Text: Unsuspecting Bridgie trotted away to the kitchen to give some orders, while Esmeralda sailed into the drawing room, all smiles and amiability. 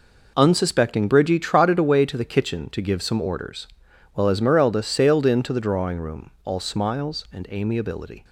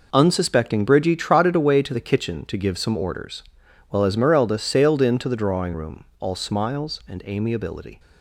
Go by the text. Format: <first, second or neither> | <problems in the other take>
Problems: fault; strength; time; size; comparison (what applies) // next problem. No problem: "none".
neither | none